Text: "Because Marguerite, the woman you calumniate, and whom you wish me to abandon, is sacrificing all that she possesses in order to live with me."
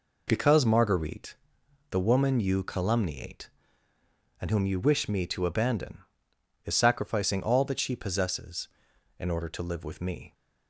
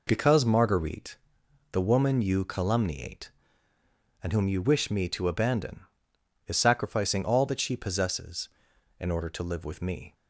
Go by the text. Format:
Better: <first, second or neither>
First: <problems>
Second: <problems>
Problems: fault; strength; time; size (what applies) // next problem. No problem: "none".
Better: neither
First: none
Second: none